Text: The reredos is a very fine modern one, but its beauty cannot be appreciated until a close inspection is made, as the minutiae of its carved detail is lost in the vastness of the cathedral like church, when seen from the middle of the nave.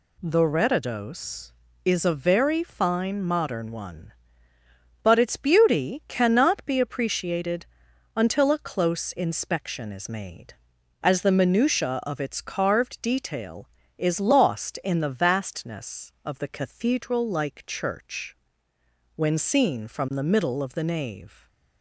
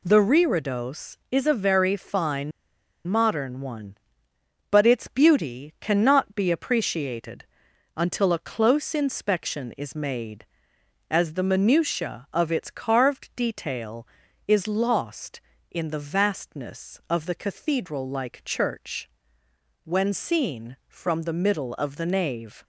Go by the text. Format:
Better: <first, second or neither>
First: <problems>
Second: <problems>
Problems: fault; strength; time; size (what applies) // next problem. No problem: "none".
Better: first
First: pauses between "appreciated" and "until"; noticeable; at 7.6 s; 0.52 s long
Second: pauses between "fine" and "modern"; noticeable; at 2.5 s; 0.56 s long // pauses between "appreciated" and "until"; noticeable; at 7.4 s; 0.52 s long